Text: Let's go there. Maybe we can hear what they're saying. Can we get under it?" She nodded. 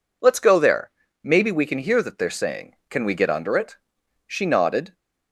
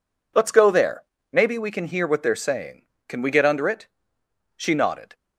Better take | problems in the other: second | says "that" for "what"; at 2.0 s

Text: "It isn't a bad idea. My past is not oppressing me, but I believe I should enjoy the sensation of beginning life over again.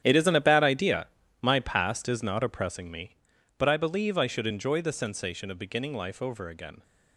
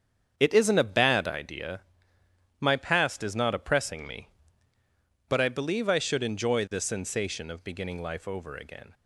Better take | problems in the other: second | gets quieter; strong; throughout; 14.5 dB // starts louder than the rest; strong; until 1.0 s; 10 dB; strong in the second

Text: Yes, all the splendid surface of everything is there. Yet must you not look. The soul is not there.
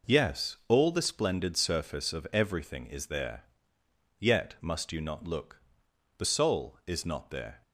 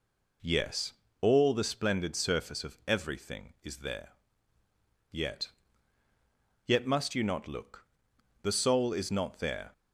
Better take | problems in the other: first | says "Yet" twice; at 6.6 s

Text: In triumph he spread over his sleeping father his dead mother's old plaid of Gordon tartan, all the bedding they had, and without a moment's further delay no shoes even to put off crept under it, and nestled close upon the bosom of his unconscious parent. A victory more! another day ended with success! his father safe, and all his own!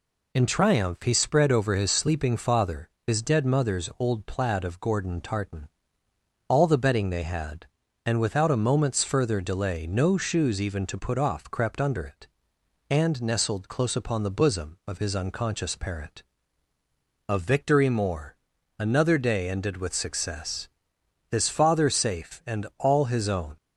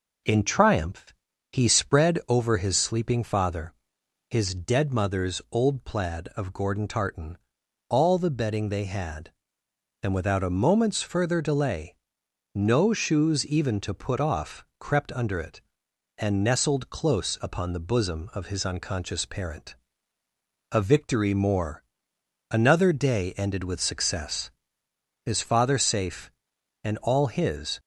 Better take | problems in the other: first | pauses between "triumph" and "he"; at 1.1 s; 0.38 s long // pauses between "father" and "his"; noticeable; at 3.7 s; 0.56 s long; slight in the first // pauses between "delay" and "no"; noticeable; at 11.9 s; 0.58 s long // stops before "own"; at 27.7 s

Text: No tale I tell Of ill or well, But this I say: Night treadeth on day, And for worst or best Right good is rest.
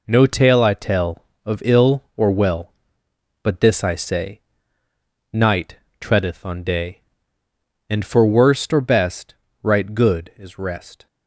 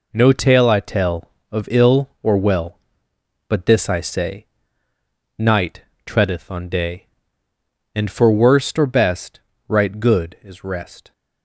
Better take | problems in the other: neither | pauses between "Night" and "treadeth"; slight; the same in both // pauses between "best" and "Right"; slight; the same in both

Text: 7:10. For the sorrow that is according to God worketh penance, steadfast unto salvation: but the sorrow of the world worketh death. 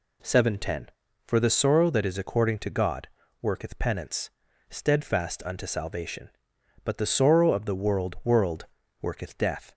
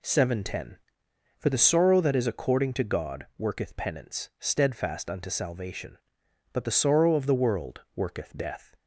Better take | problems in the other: second | pauses between "God" and "worketh"; slight; at 3.0 s; 0.34 s long // says "world" twice; at 8.2 s

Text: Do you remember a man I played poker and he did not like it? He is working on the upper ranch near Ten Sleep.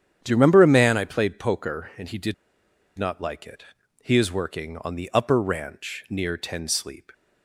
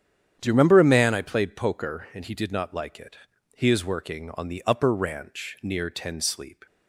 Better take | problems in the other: second | starts louder than the rest; strong; until 1.2 s; 9 dB; strong in the second // pauses between "did" and "not"; noticeable; at 2.3 s; 0.64 s long

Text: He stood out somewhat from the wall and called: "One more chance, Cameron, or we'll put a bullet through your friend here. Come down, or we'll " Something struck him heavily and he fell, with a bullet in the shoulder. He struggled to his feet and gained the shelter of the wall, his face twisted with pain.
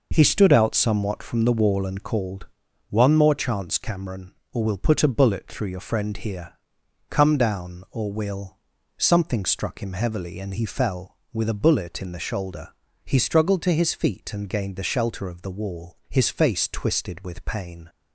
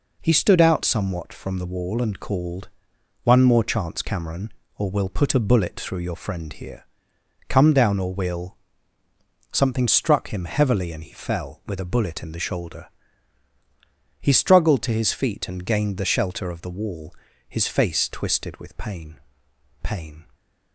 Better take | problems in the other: first | says "pain" twice; at 19.8 s

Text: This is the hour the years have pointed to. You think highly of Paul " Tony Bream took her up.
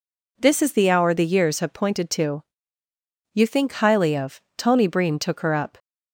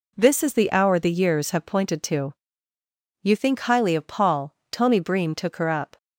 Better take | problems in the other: second | skips "Paul"; at 4.4 s

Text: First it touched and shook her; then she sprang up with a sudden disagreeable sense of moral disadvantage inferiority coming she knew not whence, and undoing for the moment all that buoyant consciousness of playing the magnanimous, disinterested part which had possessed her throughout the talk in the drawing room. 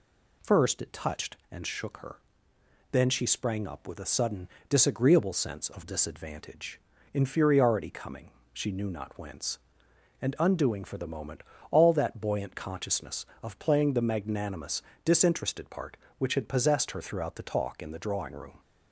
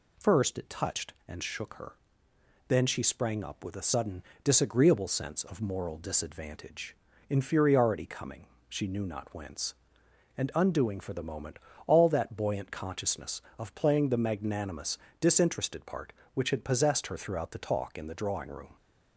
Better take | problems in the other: second | pauses between "sudden" and "disagreeable"; slight; at 4.4 s; 0.22 s long; slight in the second // skips "moral"; at 5.8 s // pauses between "disadvantage" and "inferiority"; slight; at 6.7 s; 0.32 s long; slight in the second // pauses between "coming" and "she"; slight; at 8.2 s; 0.24 s long; slight in the second // pauses between "moment" and "all"; slight; at 11.4 s; 0.30 s long; slight in the second

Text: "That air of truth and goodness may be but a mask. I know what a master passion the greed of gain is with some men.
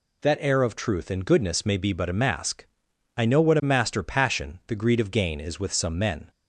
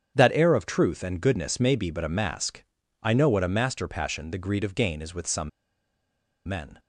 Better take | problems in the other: first | starts louder than the rest; strong; until 1.1 s; 8 dB // pauses between "some" and "men"; noticeable; at 5.4 s; 0.97 s long

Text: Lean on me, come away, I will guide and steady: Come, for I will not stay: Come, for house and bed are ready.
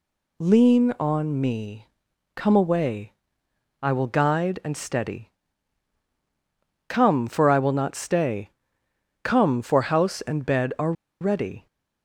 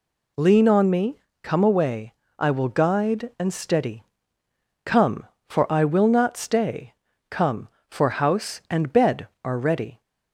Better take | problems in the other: second | pauses between "are" and "ready"; slight; at 10.9 s; 0.28 s long

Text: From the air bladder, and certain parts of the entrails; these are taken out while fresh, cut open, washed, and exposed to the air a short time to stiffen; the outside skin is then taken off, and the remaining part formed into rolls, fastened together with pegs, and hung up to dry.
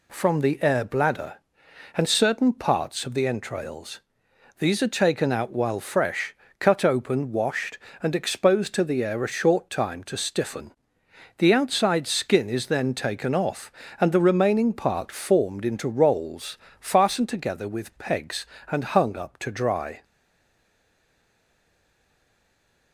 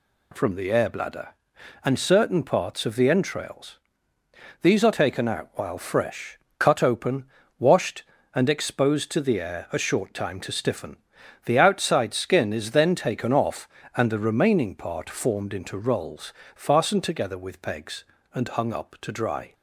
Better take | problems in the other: second | stays silent after the last word; strong; from 20.0 s on; 2.9 s long

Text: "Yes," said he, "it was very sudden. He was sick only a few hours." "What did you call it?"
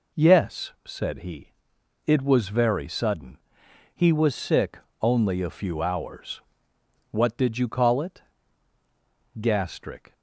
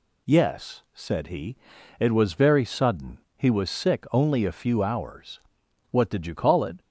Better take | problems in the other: second | pauses between "sick" and "only"; slight; at 4.7 s; 0.22 s long // goes on to say "Gastric"; noticeable; from 9.3 s on; 0.74 s long

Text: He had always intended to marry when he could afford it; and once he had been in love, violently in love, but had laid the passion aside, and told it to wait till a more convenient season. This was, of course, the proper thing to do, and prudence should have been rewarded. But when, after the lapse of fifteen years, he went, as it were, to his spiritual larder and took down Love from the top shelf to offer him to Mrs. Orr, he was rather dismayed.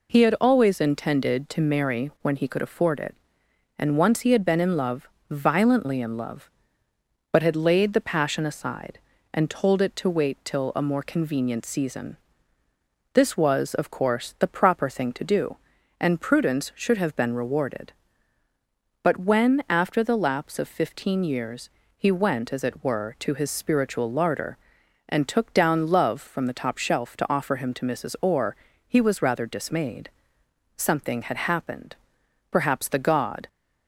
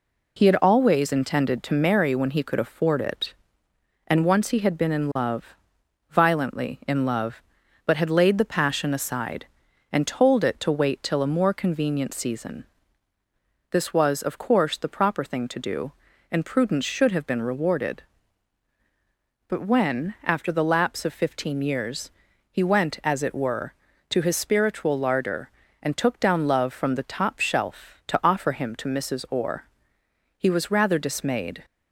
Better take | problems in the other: second | goes on to say "Something had happened Perhaps the god"; strong; from 30.7 s on; 2.7 s long

